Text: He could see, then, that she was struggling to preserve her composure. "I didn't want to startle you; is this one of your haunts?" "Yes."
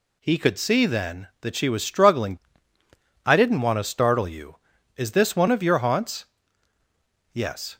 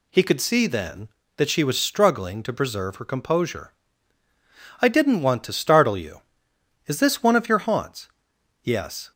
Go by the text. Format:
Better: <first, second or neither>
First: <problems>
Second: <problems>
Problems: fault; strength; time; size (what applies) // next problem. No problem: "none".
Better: second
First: skips "to preserve her composure"; at 2.7 s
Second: none